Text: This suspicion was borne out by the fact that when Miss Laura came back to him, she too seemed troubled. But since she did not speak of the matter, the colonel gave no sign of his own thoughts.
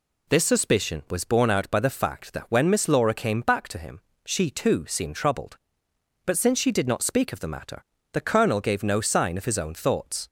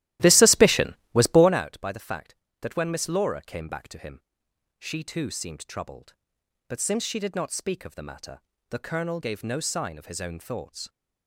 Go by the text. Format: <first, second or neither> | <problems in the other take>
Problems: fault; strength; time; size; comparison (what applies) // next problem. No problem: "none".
first | starts louder than the rest; strong; until 1.7 s; 15 dB